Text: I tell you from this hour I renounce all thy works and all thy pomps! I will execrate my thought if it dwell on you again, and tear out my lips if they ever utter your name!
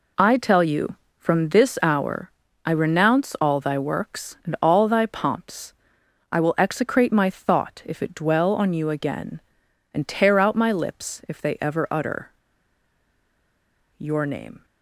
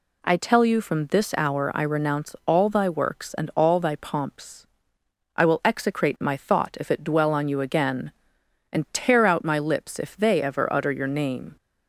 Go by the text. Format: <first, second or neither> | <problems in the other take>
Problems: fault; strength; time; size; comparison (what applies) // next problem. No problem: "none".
second | pauses between "hour" and "I"; slight; at 2.3 s; 0.34 s long // pauses between "utter" and "your"; strong; at 12.3 s; 1.6 s long